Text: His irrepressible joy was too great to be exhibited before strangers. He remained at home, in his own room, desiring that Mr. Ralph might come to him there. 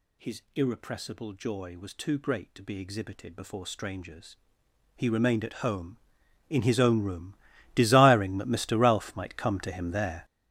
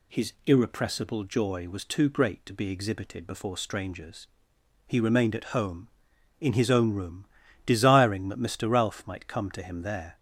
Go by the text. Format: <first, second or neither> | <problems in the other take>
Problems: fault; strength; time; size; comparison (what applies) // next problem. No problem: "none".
second | gets louder; strong; throughout; 12.5 dB // pauses between "His" and "irrepressible"; slight; at 0.4 s; 0.16 s long; slight in the second